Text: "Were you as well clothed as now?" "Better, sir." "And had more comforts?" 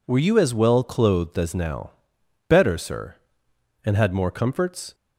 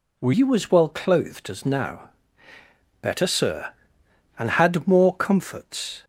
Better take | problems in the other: first | changes voice at "you"; from 0.3 s on; 5.7 s long

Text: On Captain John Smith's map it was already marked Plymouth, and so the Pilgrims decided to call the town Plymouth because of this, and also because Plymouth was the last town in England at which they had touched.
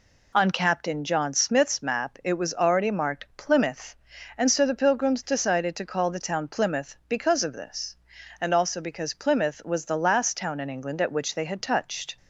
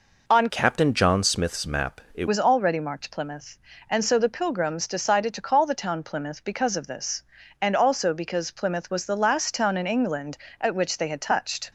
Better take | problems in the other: first | changes voice from "Captain" to "it"; from 0.4 to 2.2 s; 1.8 s long

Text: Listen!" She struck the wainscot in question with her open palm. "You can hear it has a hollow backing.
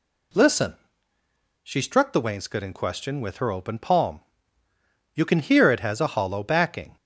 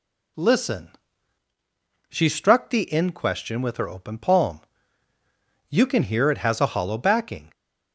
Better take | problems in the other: first | skips "wainscot"; at 2.8 s

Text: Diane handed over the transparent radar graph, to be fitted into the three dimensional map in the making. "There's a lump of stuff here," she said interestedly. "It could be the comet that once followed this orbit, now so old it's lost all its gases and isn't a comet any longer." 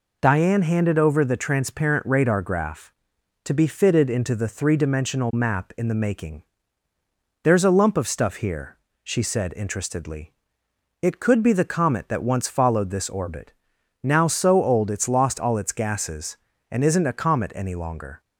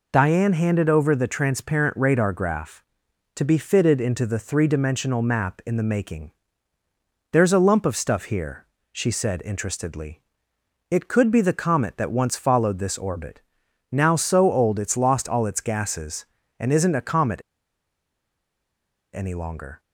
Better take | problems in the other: first | pauses between "comet" and "any"; strong; at 17.3 s; 1.7 s long

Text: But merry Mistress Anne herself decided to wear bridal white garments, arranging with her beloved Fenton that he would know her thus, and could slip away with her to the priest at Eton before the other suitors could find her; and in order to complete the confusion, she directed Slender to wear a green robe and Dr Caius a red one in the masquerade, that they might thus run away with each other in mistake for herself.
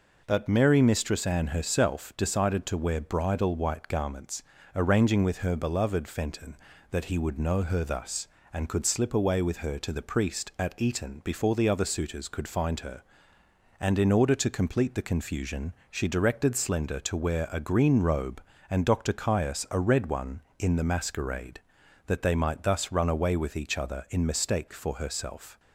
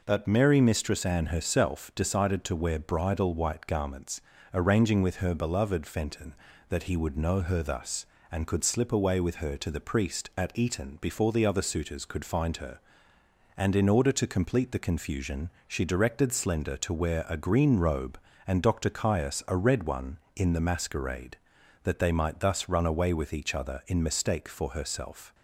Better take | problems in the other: neither | none

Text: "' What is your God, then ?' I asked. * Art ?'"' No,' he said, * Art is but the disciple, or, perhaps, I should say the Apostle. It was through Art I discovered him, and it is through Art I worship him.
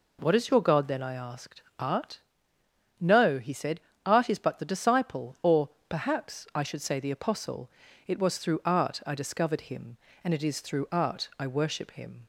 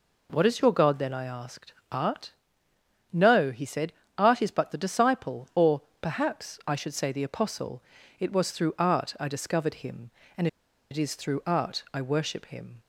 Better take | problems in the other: first | pauses between "and" and "it"; at 10.4 s; 0.44 s long

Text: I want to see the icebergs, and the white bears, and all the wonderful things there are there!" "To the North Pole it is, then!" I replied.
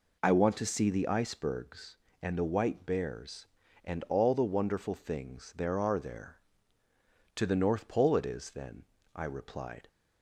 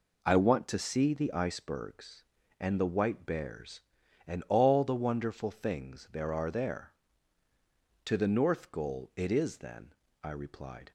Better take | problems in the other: first | says "Goal" for "Pole"; at 8.6 s

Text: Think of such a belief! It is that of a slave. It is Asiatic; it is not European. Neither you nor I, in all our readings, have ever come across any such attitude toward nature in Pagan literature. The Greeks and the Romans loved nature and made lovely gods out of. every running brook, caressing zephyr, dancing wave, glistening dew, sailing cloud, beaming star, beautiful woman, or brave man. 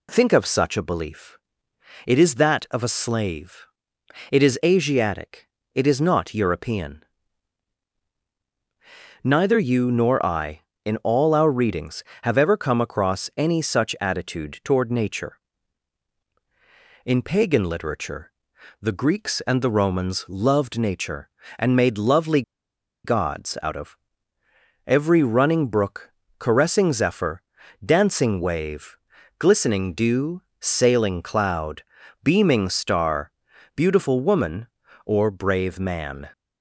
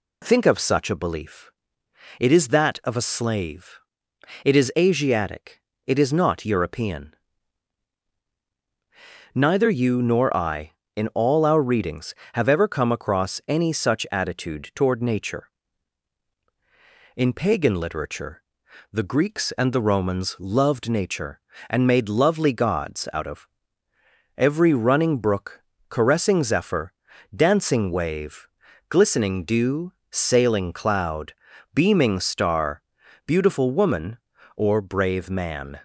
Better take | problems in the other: second | pauses between "lovely" and "gods"; noticeable; at 22.4 s; 0.62 s long

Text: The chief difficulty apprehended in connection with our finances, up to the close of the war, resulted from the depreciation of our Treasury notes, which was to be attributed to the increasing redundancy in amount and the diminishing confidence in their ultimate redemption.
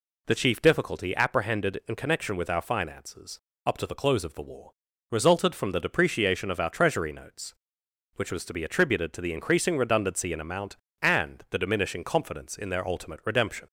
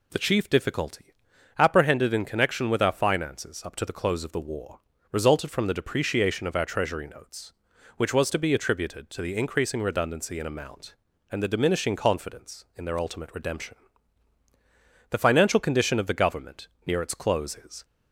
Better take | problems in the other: first | pauses between "difficulty" and "apprehended"; at 1.1 s; 0.44 s long // goes on to say "The financial condition of the Government near its close is"; strong; from 15.0 s on; 2.7 s long

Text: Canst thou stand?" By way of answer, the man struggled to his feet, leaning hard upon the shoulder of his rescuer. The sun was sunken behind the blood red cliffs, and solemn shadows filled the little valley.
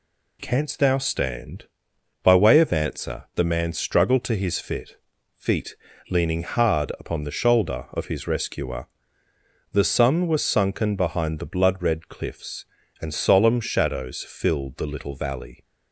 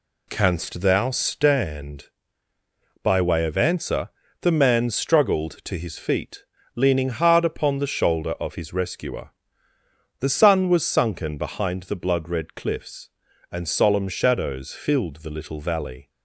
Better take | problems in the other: second | says "feet" twice; at 5.3 s

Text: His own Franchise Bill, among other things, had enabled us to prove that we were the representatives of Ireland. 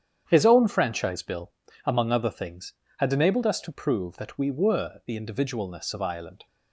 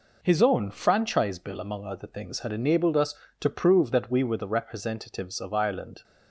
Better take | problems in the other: second | starts louder than the rest; strong; until 1.2 s; 8.5 dB // says "individualness" for "representatives"; at 5.1 s

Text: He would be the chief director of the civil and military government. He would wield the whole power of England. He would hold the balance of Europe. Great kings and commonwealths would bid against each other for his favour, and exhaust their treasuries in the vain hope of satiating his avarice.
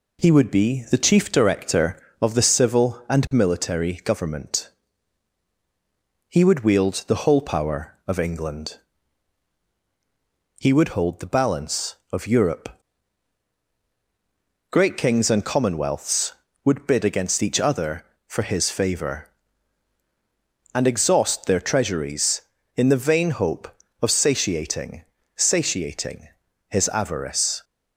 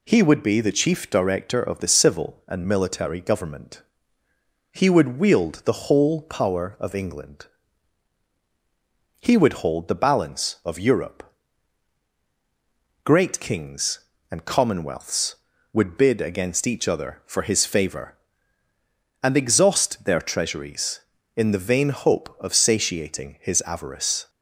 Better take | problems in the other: second | says "satiating" twice; at 25.3 s

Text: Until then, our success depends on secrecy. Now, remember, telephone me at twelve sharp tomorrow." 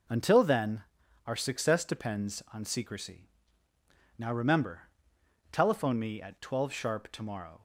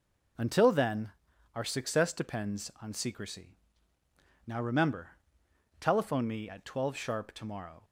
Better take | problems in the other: neither | none

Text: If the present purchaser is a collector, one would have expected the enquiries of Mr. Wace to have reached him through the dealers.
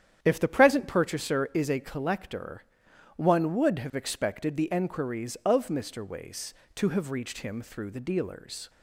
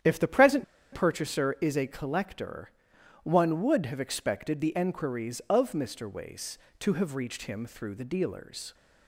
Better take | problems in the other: first | starts louder than the rest; strong; until 1.3 s; 9.5 dB; strong in the first // pauses between "present" and "purchaser"; slight; at 0.6 s; 0.29 s long

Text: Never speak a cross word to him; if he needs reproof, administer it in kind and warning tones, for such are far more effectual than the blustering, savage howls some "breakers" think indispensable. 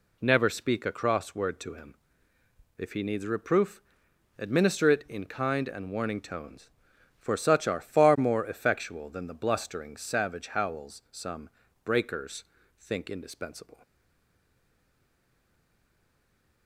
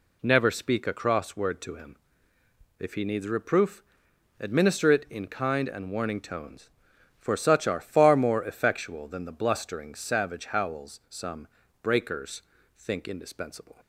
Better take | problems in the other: second | pauses between "some" and "breakers"; slight; at 11.4 s; 0.34 s long; slight in the second // pauses between "breakers" and "think"; slight; at 12.4 s; 0.34 s long; slight in the second // stays silent after the last word; strong; from 13.8 s on; 2.8 s long

